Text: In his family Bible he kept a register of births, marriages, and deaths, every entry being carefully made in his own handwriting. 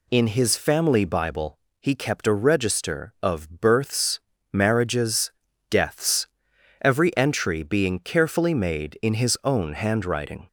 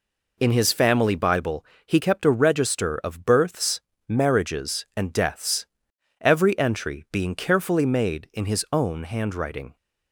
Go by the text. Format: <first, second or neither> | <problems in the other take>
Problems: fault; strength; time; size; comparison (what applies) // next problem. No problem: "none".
second | pauses between "Bible" and "he"; slight; at 1.5 s; 0.24 s long; slight in the second // skips "and"; at 5.5 s